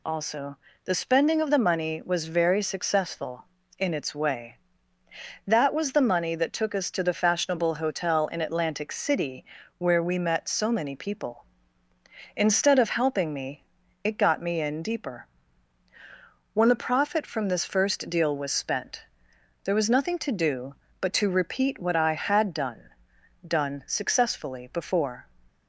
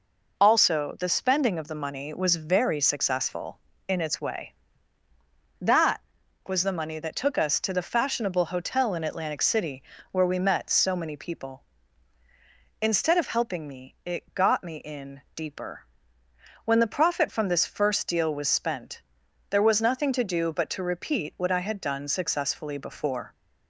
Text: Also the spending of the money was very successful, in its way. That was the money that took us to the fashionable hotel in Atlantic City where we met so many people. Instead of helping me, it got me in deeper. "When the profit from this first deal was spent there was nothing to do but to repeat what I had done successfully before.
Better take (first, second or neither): second